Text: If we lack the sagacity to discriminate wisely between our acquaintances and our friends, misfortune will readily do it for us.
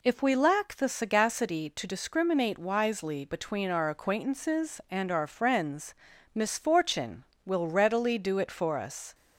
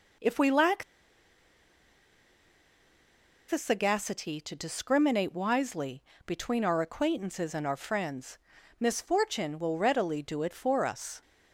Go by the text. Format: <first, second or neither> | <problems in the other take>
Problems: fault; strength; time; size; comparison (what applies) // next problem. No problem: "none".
first | pauses between "lack" and "the"; strong; at 0.8 s; 2.6 s long // pauses between "wisely" and "between"; slight; at 6.0 s; 0.24 s long